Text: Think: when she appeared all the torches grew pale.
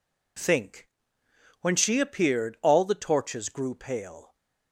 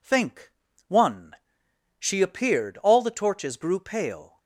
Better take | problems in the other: first | says "one" for "when"; at 0.8 s

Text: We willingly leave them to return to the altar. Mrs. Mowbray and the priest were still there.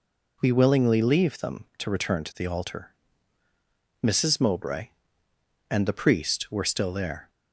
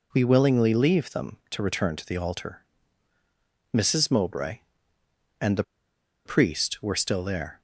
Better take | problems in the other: first | pauses between "the" and "priest"; noticeable; at 5.6 s; 0.63 s long

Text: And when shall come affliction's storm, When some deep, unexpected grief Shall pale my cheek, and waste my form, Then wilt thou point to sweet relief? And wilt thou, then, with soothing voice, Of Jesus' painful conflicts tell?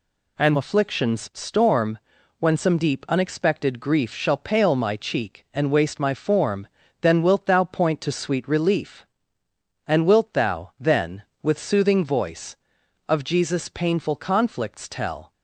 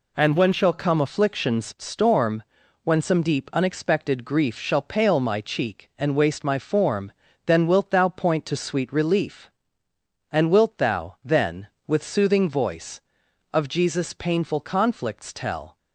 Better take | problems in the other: second | skips "when shall come"; at 0.5 s

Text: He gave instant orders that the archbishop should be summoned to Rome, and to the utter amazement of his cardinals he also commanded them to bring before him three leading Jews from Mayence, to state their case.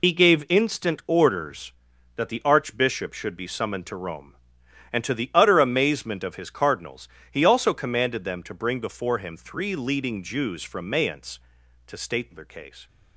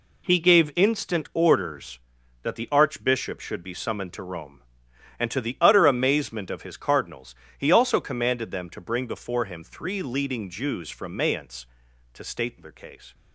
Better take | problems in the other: second | loses the start of "He"; at 0.0 s; 45 ms // pauses between "cardinals" and "he"; slight; at 7.0 s; 0.24 s long; slight in the second

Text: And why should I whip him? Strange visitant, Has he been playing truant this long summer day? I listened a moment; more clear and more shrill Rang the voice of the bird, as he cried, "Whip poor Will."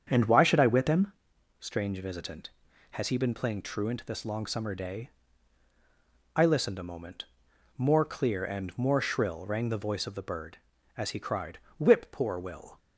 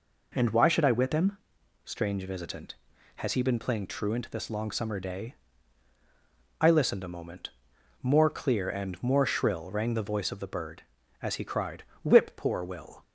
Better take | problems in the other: second | starts louder than the rest; strong; until 1.1 s; 7.5 dB

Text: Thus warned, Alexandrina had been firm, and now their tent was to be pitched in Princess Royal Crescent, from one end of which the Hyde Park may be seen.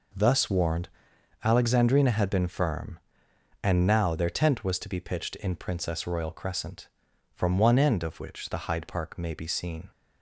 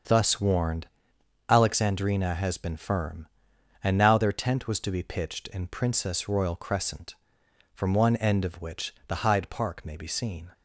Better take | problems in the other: first | starts louder than the rest; until 1.7 s; 7 dB // says "has" for "had"; at 2.3 s

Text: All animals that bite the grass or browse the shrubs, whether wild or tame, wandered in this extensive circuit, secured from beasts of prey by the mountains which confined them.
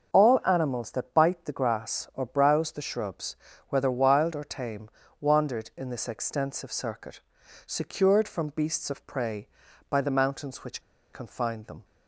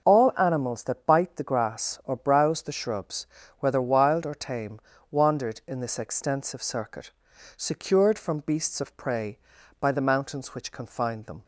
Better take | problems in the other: second | pauses between "which" and "confined"; slight; at 10.8 s; 0.32 s long

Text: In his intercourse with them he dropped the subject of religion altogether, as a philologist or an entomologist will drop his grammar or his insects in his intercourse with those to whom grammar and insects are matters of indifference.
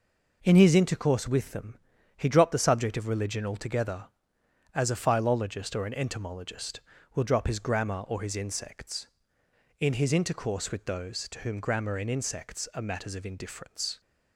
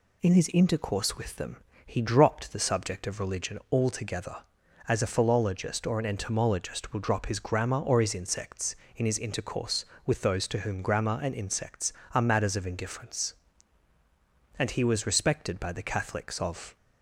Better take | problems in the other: first | pauses between "them" and "he"; slight; at 1.5 s; 0.30 s long; also in the first // goes on to say "And he was respected by the Catholics of"; strong; from 14.5 s on; 2.1 s long

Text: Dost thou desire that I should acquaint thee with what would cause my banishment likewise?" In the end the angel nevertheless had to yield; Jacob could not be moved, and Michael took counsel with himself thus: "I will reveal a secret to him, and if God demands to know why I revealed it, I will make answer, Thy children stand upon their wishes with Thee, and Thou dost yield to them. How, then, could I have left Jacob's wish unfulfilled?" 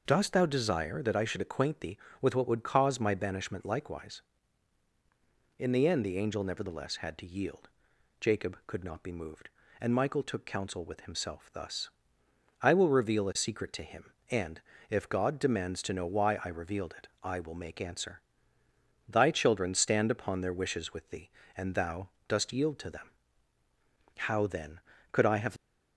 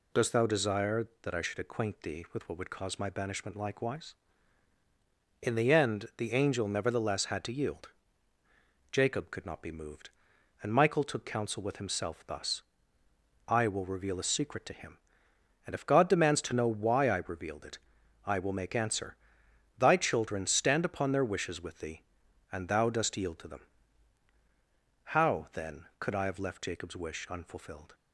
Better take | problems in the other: second | pauses between "and" and "if"; slight; at 14.6 s; 0.28 s long // pauses between "Thou" and "dost"; slight; at 22.0 s; 0.20 s long // stops before "left Jacob's wish unfulfilled"; at 25.5 s

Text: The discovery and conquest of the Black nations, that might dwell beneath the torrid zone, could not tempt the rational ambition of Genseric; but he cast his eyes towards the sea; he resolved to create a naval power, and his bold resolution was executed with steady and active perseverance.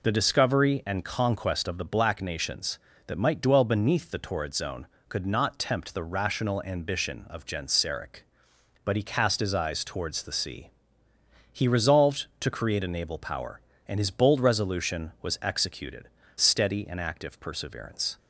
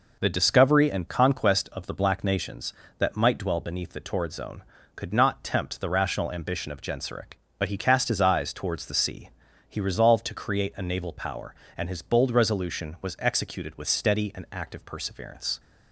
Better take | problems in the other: second | skips "with"; at 16.2 s

